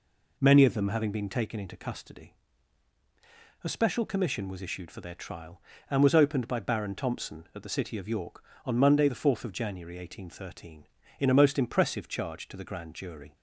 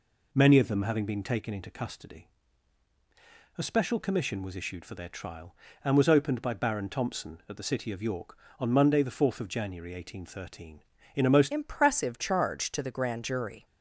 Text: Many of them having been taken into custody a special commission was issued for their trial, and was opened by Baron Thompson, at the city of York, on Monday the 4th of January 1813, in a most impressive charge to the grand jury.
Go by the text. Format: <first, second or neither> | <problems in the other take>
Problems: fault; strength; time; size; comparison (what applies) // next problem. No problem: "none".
first | pauses between "custody" and "a"; strong; at 2.2 s; 1.3 s long; strong in the first // changes voice at "impressive"; from 11.4 s on; 2.2 s long